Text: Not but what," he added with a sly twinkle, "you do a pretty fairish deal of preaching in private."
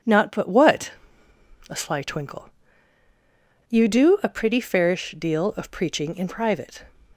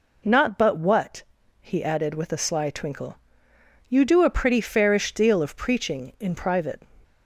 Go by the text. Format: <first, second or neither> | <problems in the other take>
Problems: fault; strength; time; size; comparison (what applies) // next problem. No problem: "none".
second | skips "he added with"; at 1.2 s